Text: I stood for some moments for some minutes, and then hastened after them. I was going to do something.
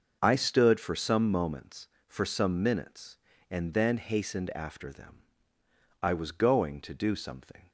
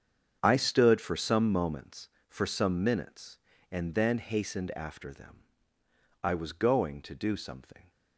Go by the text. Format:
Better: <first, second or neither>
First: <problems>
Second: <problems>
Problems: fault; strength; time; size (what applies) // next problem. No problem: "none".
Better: first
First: starts louder than the rest; until 1.2 s; 6 dB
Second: gets quieter; strong; throughout; 14.5 dB // starts louder than the rest; strong; until 1.4 s; 7.5 dB